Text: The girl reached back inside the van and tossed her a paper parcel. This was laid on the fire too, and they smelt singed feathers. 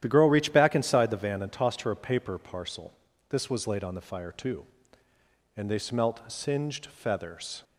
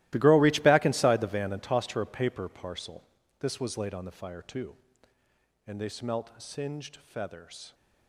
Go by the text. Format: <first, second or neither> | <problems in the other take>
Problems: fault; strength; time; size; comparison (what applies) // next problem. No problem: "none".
first | gets quieter; strong; throughout; 17 dB // starts louder than the rest; strong; until 1.1 s; 16.5 dB; strong in the first